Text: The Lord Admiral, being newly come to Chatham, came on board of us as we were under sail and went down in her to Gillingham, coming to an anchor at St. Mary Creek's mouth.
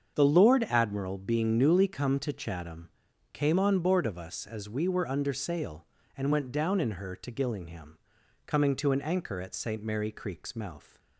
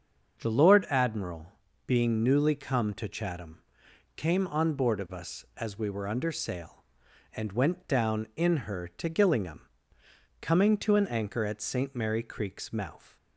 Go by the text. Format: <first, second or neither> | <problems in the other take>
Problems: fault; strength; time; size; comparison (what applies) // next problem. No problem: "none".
neither | starts louder than the rest; the same in both